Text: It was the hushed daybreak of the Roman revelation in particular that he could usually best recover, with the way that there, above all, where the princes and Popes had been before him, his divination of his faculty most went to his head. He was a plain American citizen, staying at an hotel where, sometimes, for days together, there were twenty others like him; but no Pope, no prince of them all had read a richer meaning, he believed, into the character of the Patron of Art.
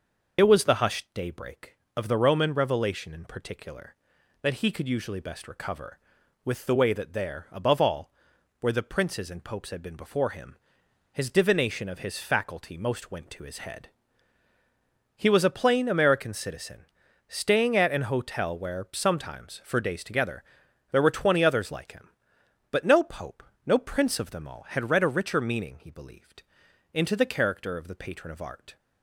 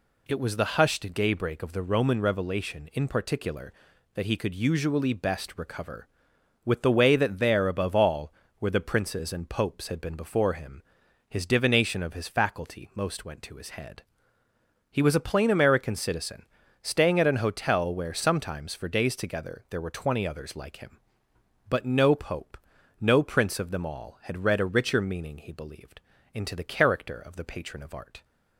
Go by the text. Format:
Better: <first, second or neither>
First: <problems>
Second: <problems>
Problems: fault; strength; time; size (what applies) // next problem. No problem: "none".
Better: second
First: loses the start of "It"; at 0.3 s; 50 ms // starts louder than the rest; noticeable; until 1.4 s; 6 dB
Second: none